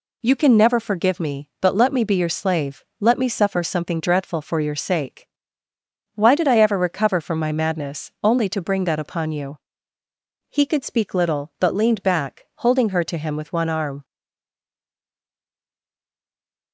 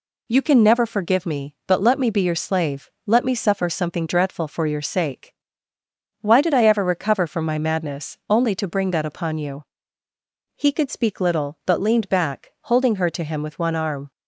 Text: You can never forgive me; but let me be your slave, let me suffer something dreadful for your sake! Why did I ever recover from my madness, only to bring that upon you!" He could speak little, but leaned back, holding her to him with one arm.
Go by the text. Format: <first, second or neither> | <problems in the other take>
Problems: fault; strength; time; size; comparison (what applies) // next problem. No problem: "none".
second | stays silent after the last word; strong; from 14.0 s on; 2.7 s long